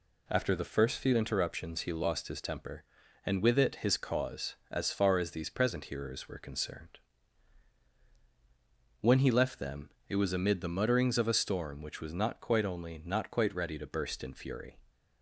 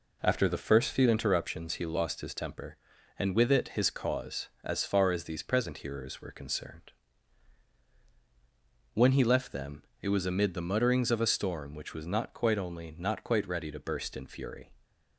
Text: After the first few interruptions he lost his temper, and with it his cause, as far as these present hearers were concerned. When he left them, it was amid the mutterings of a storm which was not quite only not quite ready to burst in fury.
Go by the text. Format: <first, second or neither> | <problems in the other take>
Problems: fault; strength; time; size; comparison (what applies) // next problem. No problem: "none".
first | starts louder than the rest; until 1.6 s; 4 dB